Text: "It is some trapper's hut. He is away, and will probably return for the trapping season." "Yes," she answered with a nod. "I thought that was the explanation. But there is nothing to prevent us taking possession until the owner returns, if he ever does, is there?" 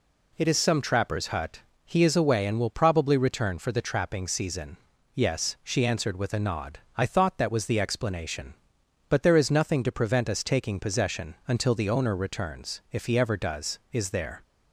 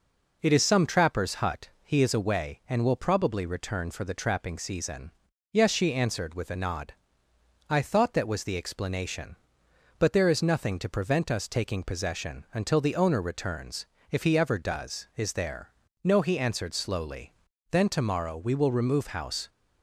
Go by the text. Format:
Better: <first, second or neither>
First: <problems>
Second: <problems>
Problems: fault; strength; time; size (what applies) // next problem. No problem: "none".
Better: first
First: none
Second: goes on to say "No he answered slowly Then tomorrow we will remove house"; strong; from 16.0 s on; 3.4 s long